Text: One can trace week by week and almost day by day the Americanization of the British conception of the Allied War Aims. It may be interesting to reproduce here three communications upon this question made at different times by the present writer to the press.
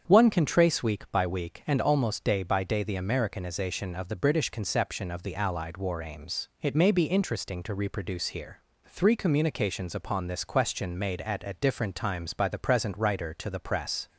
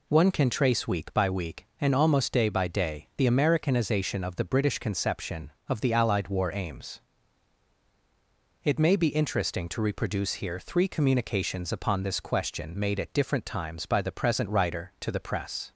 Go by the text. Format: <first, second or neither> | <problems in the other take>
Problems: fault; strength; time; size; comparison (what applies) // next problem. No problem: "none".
second | starts louder than the rest; strong; until 1.0 s; 7.5 dB // pauses between "here" and "three"; slight; at 8.6 s; 0.26 s long // says "at" twice; at 11.4 s